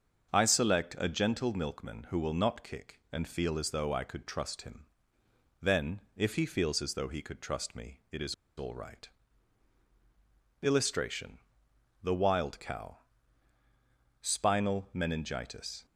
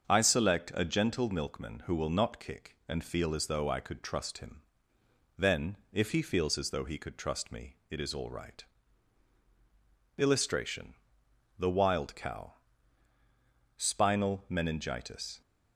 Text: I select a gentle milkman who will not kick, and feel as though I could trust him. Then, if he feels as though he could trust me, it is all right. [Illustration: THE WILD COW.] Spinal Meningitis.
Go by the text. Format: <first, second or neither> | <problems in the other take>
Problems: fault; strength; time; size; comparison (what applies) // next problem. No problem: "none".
second | starts louder than the rest; until 1.3 s; 6.5 dB; also in the second // pauses between "is" and "all"; slight; at 8.3 s; 0.22 s long